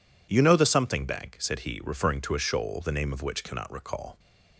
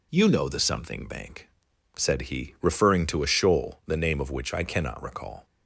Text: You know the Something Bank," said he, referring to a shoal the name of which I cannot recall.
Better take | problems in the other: second | skips "I"; at 3.4 s

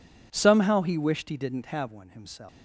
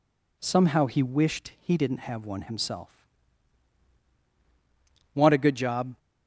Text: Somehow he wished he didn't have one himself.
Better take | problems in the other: first | goes on to say "Want a good job"; noticeable; from 5.1 s on; 0.84 s long

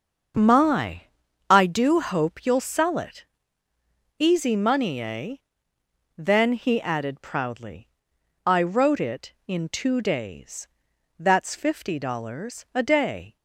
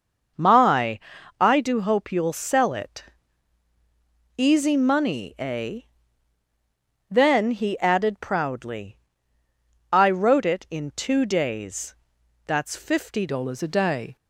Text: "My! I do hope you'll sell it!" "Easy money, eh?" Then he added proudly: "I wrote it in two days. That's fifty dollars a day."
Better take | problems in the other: first | starts louder than the rest; until 1.7 s; 6 dB; also in the first // changes voice at "dollars"; from 13.2 s on; 0.9 s long

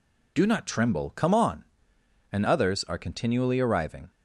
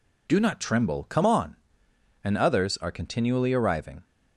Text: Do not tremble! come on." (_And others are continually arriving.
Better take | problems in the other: neither | none

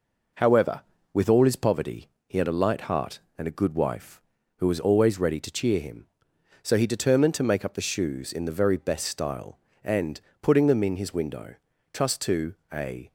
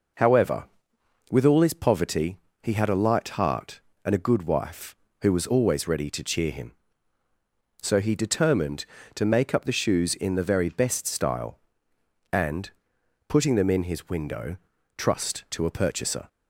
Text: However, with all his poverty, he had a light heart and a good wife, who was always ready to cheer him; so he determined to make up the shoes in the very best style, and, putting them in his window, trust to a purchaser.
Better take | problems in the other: second | pauses between "to" and "a"; slight; at 12.5 s; 0.16 s long // stops before "purchaser"; at 13.0 s

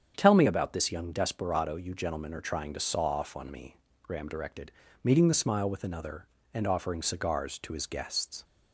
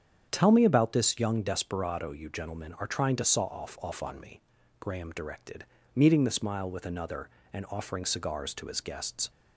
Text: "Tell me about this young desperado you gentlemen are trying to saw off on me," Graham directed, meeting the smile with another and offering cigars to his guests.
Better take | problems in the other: first | starts louder than the rest; strong; until 1.3 s; 8 dB; strong in the first // says "off" twice; at 3.7 s

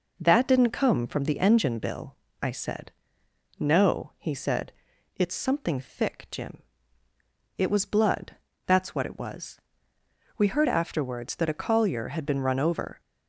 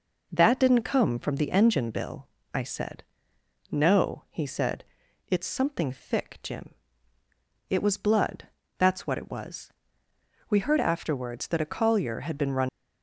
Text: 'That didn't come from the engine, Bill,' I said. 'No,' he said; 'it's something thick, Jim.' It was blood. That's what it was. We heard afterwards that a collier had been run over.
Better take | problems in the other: first | stops before "over"; at 12.6 s

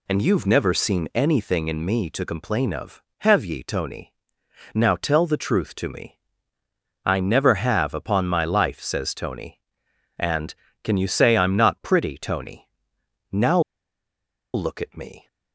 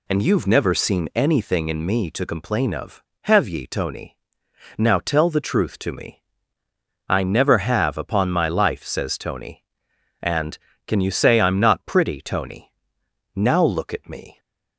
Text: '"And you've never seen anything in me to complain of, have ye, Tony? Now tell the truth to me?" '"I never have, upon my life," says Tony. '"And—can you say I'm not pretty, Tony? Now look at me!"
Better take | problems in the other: second | pauses between "Now" and "look"; noticeable; at 13.5 s; 0.94 s long

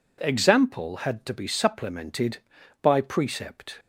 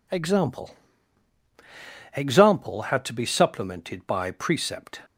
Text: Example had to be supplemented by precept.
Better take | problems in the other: first | says "Example" twice; at 2.1 s

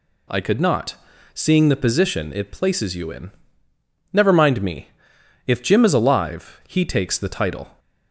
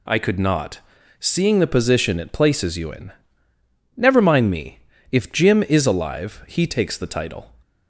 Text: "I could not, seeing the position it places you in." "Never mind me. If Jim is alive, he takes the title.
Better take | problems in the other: neither | none

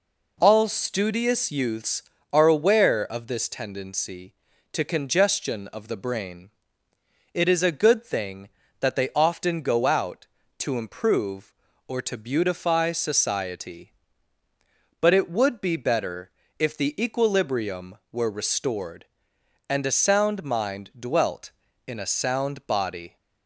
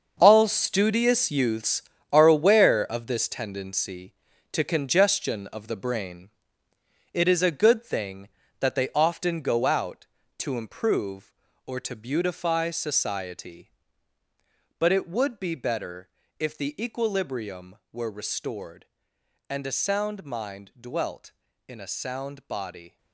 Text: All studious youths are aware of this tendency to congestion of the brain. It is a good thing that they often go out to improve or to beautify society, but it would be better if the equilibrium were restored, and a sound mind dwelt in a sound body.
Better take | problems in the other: first | gets quieter; strong; throughout; 11.5 dB // pauses between "better" and "if"; slight; at 16.0 s; 0.30 s long; slight in the first

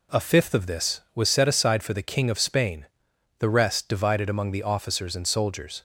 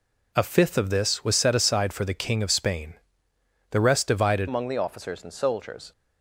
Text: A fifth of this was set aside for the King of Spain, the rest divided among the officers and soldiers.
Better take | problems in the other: first | changes voice at "among"; from 4.4 s on; 1.5 s long

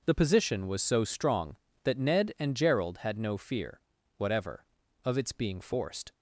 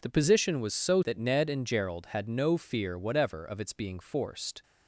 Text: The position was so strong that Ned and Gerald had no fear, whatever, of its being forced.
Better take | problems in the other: first | skips "strong"; at 1.0 s

